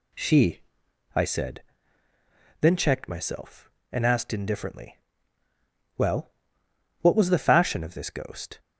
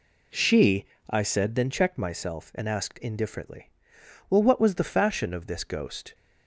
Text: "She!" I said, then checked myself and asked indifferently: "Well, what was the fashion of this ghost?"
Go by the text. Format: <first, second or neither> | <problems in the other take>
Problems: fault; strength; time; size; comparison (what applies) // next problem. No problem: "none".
first | starts louder than the rest; slight; until 1.6 s; 2 dB